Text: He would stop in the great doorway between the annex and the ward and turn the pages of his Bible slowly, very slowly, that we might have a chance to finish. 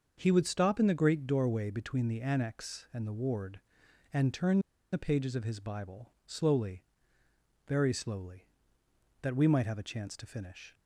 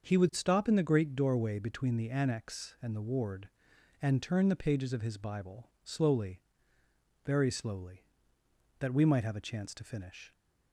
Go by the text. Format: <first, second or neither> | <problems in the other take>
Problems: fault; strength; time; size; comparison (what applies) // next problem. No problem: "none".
second | starts louder than the rest; until 1.1 s; 6.5 dB; also in the second // pauses between "turn" and "the"; slight; at 4.5 s; 0.33 s long // pauses between "Bible" and "slowly"; slight; at 6.0 s; 0.16 s long; slight in the second